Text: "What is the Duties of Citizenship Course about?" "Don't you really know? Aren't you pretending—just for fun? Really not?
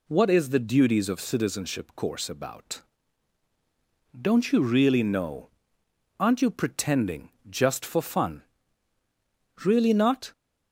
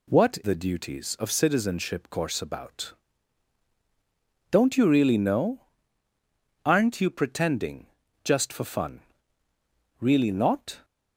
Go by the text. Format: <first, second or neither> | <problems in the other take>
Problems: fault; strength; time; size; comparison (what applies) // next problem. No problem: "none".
first | skips "is"; at 0.4 s